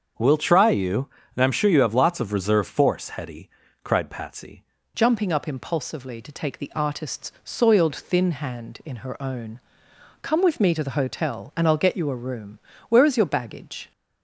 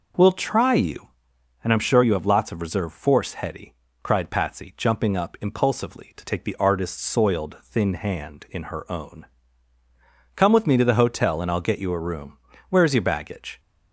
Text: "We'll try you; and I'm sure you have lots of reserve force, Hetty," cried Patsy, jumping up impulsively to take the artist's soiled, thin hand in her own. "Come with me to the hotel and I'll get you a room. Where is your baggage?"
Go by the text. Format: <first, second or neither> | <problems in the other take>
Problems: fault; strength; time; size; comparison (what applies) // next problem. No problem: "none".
second | starts louder than the rest; until 1.4 s; 6.5 dB // changes voice at "jumping"; from 4.9 s on; 9.0 s long